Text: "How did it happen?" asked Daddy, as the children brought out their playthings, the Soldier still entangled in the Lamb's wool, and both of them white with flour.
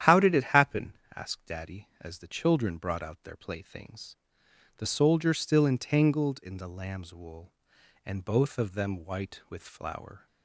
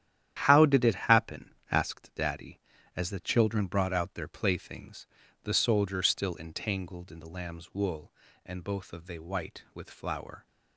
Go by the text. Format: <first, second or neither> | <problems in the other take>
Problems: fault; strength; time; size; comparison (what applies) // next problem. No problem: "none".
first | starts louder than the rest; strong; until 1.4 s; 11 dB; strong in the first // says "they" for "them"; at 9.0 s